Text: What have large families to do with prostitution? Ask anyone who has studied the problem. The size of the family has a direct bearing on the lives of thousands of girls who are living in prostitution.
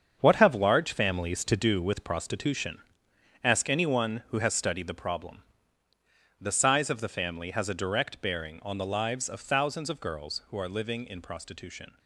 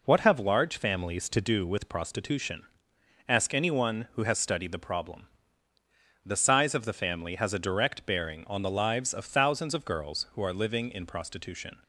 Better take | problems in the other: second | gets quieter; strong; throughout; 9.5 dB

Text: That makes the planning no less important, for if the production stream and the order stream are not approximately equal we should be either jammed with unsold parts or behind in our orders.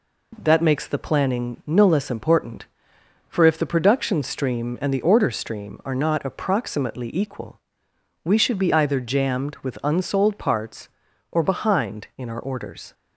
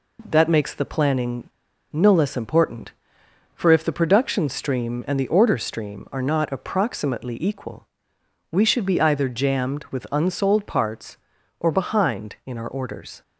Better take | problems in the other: first | pauses between "planning" and "no"; at 1.4 s; 0.43 s long // pauses between "equal" and "we"; noticeable; at 7.8 s; 0.66 s long; noticeable in the first

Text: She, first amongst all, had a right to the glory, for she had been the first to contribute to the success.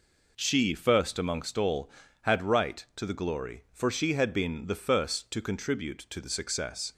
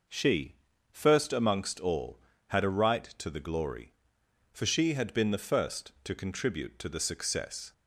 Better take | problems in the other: second | skips "a"; at 2.4 s

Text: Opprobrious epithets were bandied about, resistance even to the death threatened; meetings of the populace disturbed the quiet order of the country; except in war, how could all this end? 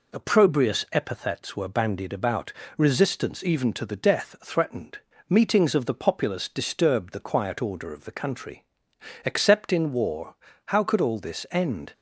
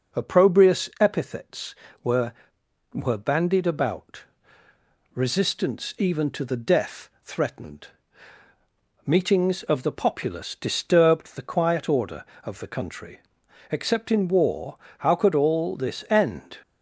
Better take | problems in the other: first | says "were" twice; at 2.9 s // pauses between "death" and "threatened"; slight; at 7.0 s; 0.16 s long

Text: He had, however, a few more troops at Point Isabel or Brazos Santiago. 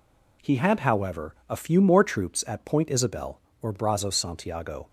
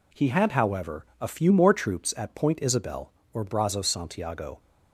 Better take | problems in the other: neither | none

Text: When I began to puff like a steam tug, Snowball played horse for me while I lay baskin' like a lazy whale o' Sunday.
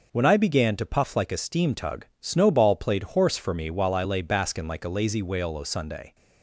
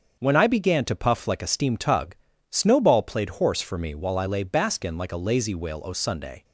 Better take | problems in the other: neither | starts louder than the rest; the same in both

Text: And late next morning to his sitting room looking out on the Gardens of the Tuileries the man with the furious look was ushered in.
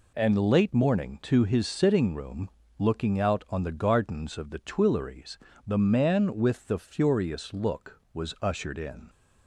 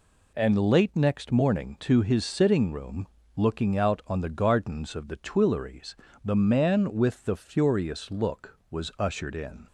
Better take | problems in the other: second | skips "next"; at 0.7 s // pauses between "room" and "looking"; slight; at 2.4 s; 0.28 s long; slight in the second // pauses between "Tuileries" and "the"; slight; at 5.3 s; 0.30 s long; slight in the second

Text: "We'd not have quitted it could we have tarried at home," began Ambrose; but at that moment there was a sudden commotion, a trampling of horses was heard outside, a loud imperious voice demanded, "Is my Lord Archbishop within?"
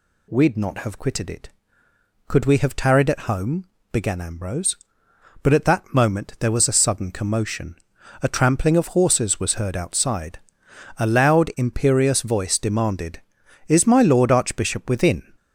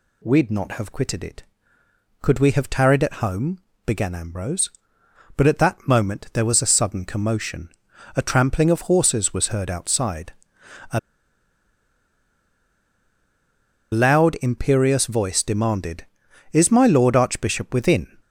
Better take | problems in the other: first | pauses between "a" and "loud"; strong; at 10.9 s; 2.9 s long

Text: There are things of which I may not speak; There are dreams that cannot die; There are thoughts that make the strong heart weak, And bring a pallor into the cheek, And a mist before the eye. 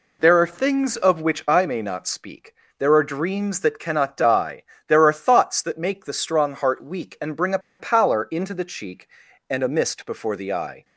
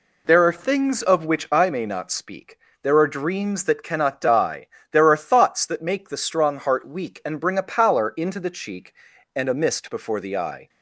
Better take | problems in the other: second | pauses between "a" and "pallor"; slight; at 7.5 s; 0.21 s long

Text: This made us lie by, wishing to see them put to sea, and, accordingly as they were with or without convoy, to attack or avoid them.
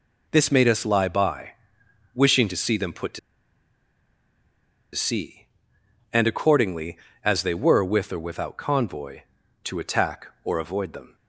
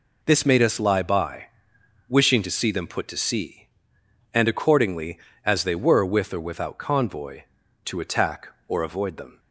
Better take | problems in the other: second | pauses between "to" and "sea"; strong; at 3.1 s; 1.7 s long

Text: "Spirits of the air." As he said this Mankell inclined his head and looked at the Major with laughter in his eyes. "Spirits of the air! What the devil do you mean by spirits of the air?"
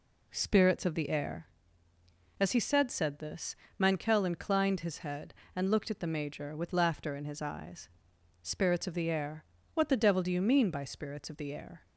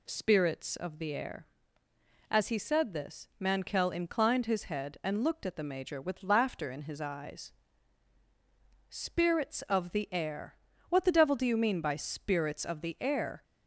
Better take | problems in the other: second | says "said" twice; at 2.9 s // pauses between "this" and "Mankell"; slight; at 3.5 s; 0.24 s long

